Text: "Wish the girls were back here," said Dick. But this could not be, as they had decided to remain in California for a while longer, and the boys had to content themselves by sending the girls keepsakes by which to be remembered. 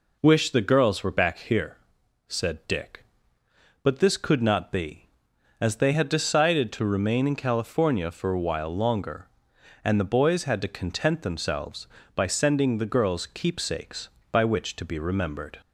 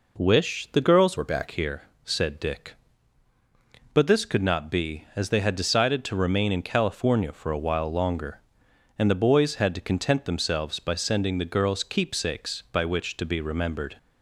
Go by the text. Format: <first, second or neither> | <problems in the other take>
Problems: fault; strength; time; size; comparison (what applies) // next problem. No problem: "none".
first | changes voice from "were" to "back"; from 1.1 to 1.4 s; 0.3 s long